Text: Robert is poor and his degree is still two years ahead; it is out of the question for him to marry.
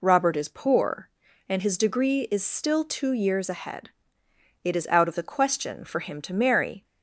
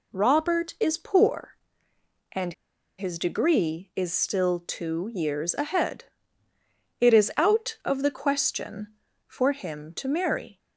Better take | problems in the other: first | pauses between "and" and "his"; noticeable; at 2.5 s; 0.46 s long

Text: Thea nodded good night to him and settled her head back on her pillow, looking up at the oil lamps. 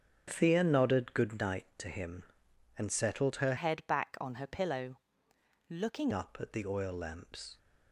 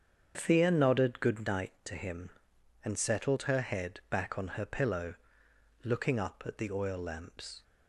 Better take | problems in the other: second | starts louder than the rest; strong; until 1.2 s; 8.5 dB; strong in the second // changes voice from "head" to "looking"; from 3.5 to 6.1 s; 2.6 s long

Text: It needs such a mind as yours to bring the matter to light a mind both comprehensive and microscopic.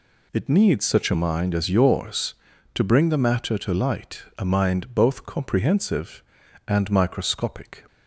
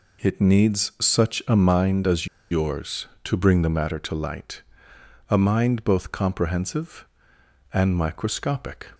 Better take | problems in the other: first | pauses between "as" and "yours"; slight; at 2.2 s; 0.25 s long // pauses between "light" and "a"; noticeable; at 4.6 s; 0.68 s long; slight in the first

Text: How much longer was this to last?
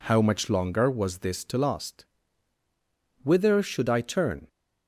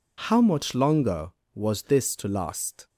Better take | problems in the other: second | goes on to say "Whither should I turn"; noticeable; from 3.2 s on; 1.2 s long

